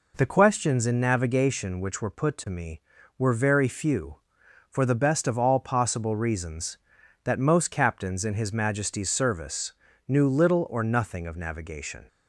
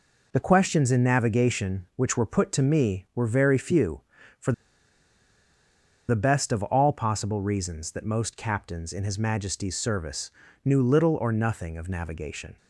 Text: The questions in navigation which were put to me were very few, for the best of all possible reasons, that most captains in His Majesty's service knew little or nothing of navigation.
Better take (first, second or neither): first